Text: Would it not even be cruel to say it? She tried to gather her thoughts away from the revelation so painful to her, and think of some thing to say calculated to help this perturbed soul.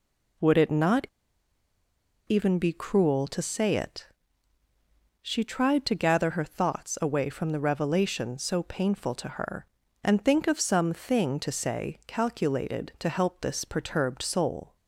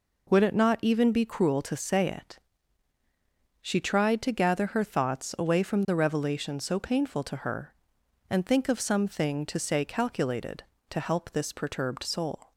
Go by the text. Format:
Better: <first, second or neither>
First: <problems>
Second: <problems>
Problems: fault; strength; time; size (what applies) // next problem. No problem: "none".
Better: second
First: pauses between "not" and "even"; at 1.0 s; 1.1 s long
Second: none